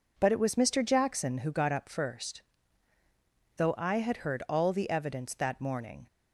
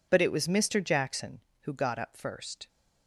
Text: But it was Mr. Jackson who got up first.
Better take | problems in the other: second | goes on to say "Though I had heard all the evidence that morning"; strong; from 3.5 s on; 2.4 s long

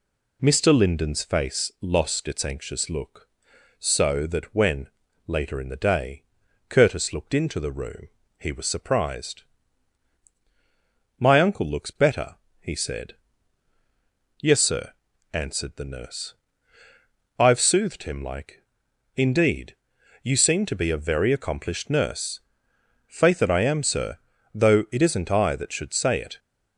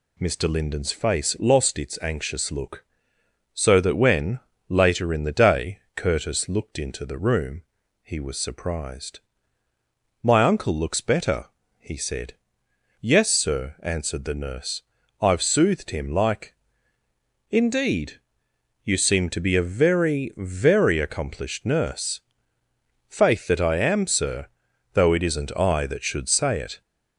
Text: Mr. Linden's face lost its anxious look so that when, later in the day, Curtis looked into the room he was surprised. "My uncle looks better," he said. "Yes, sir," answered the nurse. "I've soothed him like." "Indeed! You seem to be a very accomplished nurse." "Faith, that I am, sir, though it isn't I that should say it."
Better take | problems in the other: first | pauses between "room" and "he"; at 7.6 s; 0.42 s long; slight in the first // says "very" twice; at 20.3 s

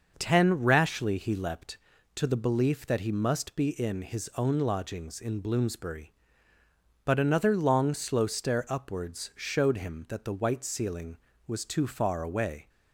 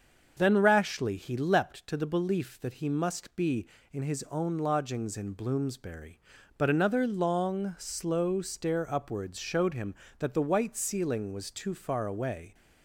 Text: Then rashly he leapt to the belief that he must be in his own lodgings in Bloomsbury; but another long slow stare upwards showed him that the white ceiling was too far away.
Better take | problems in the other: second | starts louder than the rest; noticeable; until 1.1 s; 6 dB; also in the second // says "Ten" for "Then"; at 0.1 s

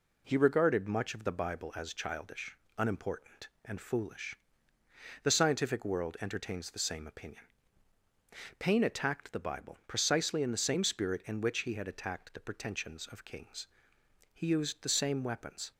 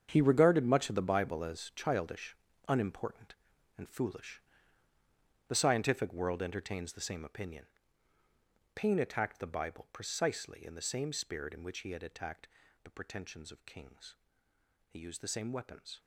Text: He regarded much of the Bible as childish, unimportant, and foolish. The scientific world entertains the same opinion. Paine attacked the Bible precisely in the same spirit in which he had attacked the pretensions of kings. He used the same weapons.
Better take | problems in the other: first | gets quieter; strong; throughout; 13.5 dB // pauses between "attacked" and "the"; slight; at 12.4 s; 0.34 s long

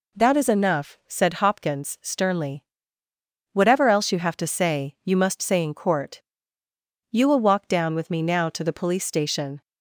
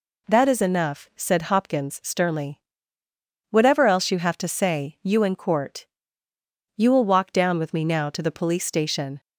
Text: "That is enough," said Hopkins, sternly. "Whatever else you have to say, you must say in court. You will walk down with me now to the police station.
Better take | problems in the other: first | skips "must say"; at 5.2 s

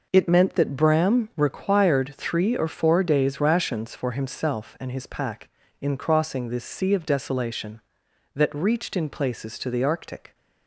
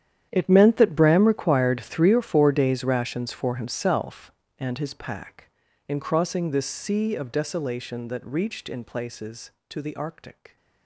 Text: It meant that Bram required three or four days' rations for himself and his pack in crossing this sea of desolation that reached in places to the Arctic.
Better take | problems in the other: first | gets quieter; strong; throughout; 16.5 dB

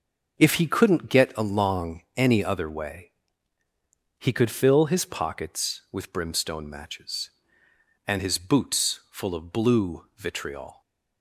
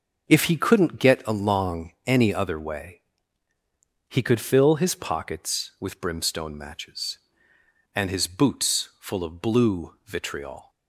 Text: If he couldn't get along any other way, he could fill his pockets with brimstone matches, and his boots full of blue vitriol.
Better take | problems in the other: neither | starts louder than the rest; the same in both // pauses between "along" and "any"; slight; the same in both

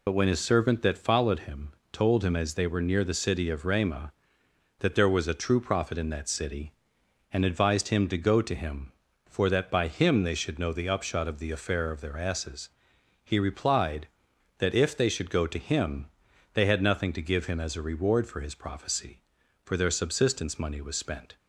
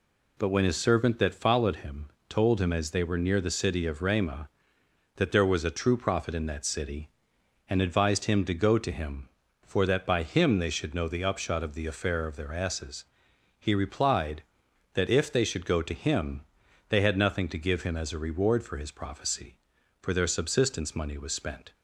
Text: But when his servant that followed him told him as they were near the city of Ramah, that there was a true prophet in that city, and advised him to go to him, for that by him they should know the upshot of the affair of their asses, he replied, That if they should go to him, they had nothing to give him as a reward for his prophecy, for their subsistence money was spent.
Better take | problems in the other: second | loses the start of "But"; at 0.0 s; 55 ms // pauses between "him" and "told"; slight; at 1.7 s; 0.20 s long; slight in the second

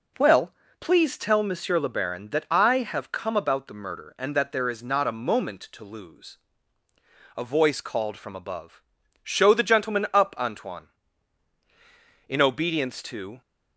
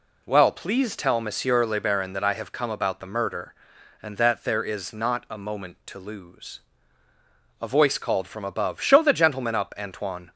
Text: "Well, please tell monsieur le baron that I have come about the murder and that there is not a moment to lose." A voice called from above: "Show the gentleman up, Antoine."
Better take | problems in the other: second | goes on to say "In obedience to"; noticeable; from 12.2 s on; 1.1 s long

